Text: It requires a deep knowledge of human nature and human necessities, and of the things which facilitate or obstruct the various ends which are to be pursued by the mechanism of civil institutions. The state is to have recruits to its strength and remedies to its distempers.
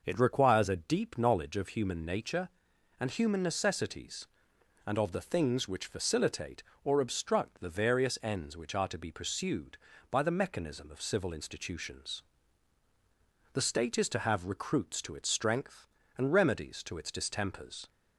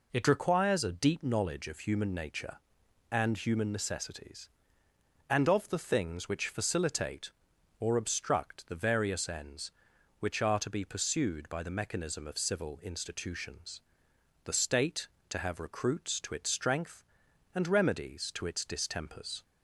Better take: first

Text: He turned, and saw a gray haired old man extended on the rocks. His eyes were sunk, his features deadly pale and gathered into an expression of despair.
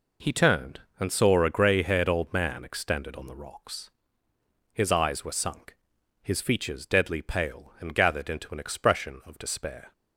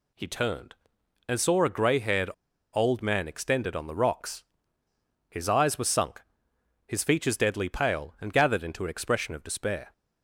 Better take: first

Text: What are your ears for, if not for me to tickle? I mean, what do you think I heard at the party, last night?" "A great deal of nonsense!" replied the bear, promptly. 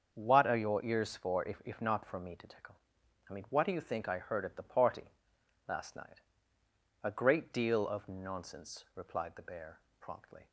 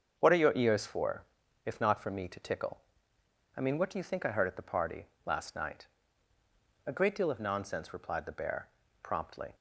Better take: second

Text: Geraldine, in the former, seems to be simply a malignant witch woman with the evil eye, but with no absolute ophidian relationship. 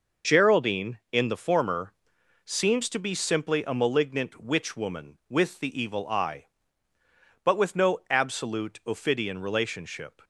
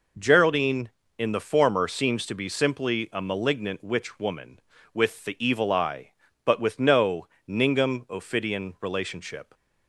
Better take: first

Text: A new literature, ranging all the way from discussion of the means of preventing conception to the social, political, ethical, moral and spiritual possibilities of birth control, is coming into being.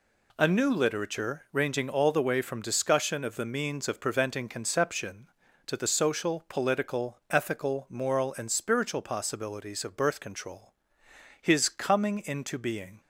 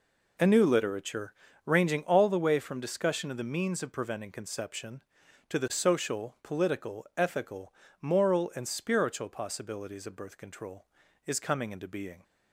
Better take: second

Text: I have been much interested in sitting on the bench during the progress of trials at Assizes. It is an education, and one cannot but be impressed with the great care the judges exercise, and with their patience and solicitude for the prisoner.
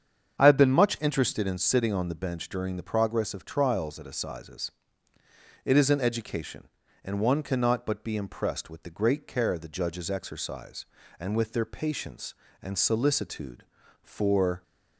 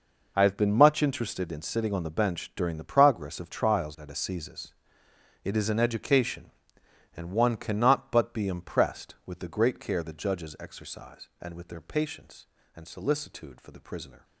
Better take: second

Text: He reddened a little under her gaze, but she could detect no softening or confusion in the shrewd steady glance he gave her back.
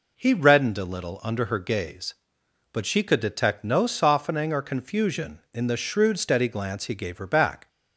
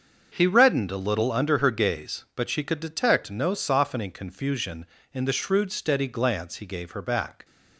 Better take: first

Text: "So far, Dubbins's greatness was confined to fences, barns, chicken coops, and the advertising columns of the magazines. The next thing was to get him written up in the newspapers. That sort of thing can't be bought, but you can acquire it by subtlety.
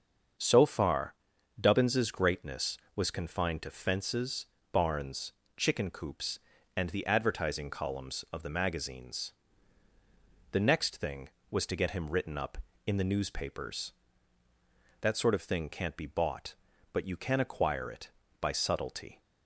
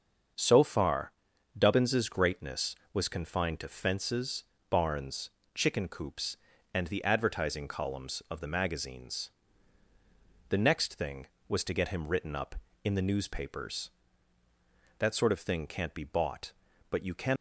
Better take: first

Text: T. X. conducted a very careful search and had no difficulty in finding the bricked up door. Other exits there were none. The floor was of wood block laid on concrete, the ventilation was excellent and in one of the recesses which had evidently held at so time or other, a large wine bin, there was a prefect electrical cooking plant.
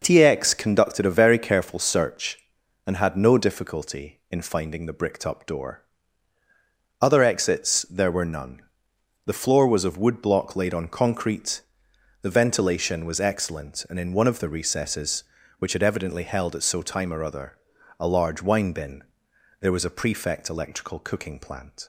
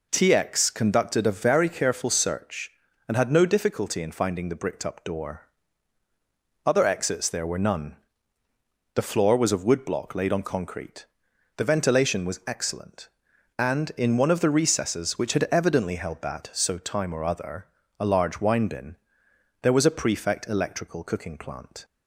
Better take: first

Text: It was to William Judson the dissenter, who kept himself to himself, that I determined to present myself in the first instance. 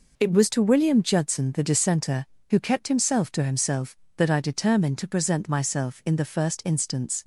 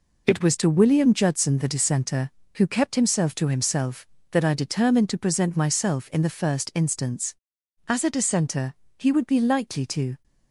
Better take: first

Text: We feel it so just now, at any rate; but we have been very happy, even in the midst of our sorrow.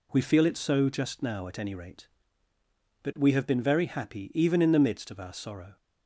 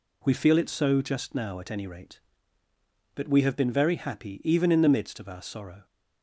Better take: neither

